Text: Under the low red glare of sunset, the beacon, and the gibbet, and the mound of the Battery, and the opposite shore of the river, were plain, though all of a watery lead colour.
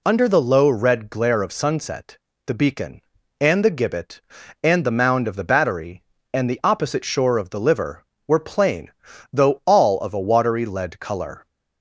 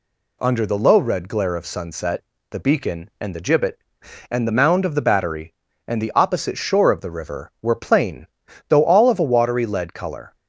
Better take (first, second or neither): second